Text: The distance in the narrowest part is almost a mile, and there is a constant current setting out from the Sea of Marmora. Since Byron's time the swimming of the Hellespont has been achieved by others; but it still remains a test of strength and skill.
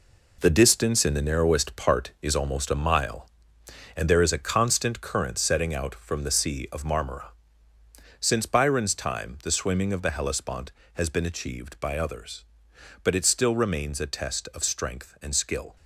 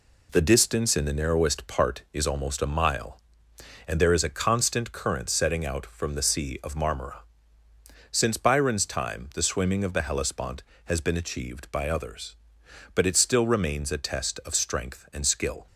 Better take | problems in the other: second | gets quieter; strong; throughout; 8.5 dB

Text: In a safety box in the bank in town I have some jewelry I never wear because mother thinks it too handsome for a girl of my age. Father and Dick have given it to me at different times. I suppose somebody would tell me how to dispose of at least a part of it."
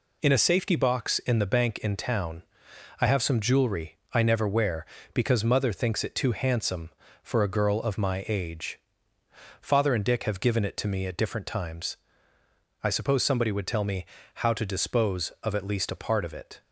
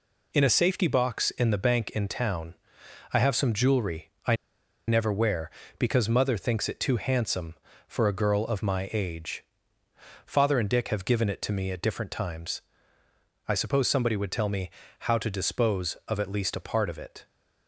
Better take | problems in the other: first | pauses between "town" and "I"; noticeable; at 2.5 s; 0.62 s long; noticeable in the first // pauses between "jewelry" and "I"; slight; at 4.1 s; 0.16 s long; slight in the first // pauses between "I" and "never"; noticeable; at 4.3 s; 0.52 s long // pauses between "me" and "how"; slight; at 14.7 s; 0.30 s long; slight in the first

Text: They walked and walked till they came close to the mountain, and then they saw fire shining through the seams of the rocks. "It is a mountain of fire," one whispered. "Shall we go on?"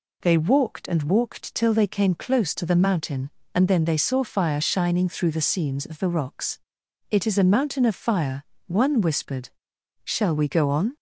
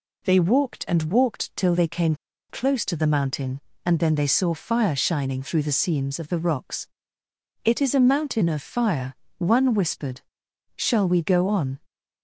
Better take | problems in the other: first | pauses between "came" and "close"; slight; at 2.1 s; 0.34 s long

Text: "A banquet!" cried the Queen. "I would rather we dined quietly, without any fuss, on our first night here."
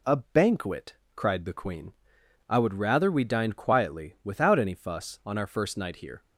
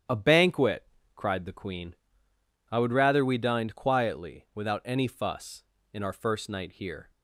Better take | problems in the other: first | starts louder than the rest; strong; until 1.4 s; 10 dB // says "in" for "on"; at 5.9 s

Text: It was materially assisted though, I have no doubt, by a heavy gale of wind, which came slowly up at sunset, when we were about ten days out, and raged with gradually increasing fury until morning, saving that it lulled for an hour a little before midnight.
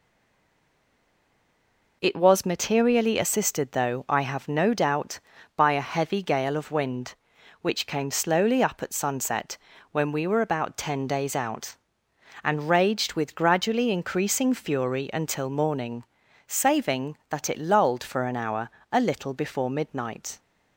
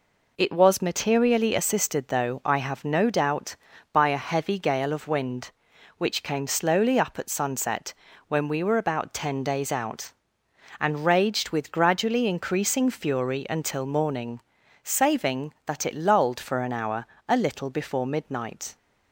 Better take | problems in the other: second | stays silent before the first word; noticeable; until 2.0 s; 2.0 s long // pauses between "hour" and "a"; slight; at 18.6 s; 0.22 s long; slight in the second

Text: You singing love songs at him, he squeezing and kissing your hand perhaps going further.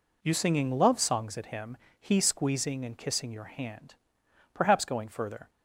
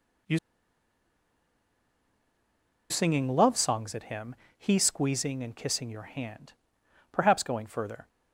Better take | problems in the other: first | pauses between "You" and "singing"; strong; at 0.3 s; 2.5 s long // pauses between "hand" and "perhaps"; noticeable; at 6.5 s; 0.60 s long; noticeable in the first

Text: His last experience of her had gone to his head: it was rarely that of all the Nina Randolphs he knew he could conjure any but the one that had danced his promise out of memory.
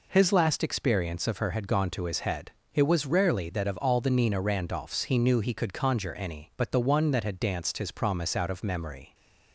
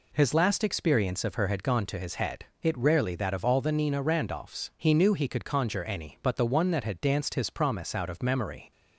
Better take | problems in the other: first | skips "was"; at 2.7 s

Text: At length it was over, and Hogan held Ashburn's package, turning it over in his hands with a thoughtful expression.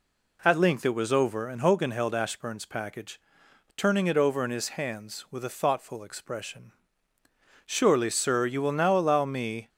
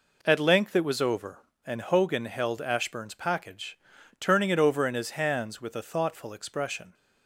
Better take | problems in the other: second | goes on to say "Surely sir you will now allow me"; strong; from 7.6 s on; 2.0 s long

